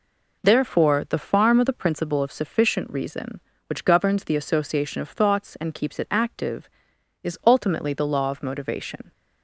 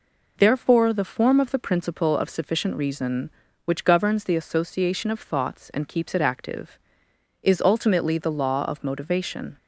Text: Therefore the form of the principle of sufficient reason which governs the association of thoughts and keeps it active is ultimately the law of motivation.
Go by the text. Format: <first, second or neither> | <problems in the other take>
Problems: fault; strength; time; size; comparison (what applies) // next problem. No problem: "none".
second | says "farm" for "form"; at 1.1 s